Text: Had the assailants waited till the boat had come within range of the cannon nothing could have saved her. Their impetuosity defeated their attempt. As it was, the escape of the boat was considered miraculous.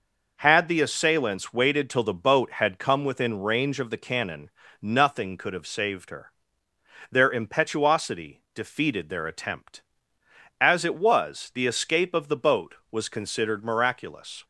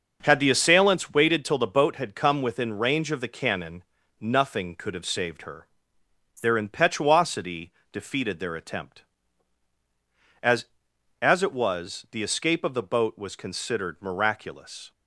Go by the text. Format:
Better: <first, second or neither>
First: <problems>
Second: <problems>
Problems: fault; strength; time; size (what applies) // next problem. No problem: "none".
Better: first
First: pauses between "cannon" and "nothing"; slight; at 4.5 s; 0.32 s long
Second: pauses between "cannon" and "nothing"; at 3.8 s; 0.40 s long // pauses between "impetuosity" and "defeated"; slight; at 7.7 s; 0.20 s long // says "As" twice; at 11.2 s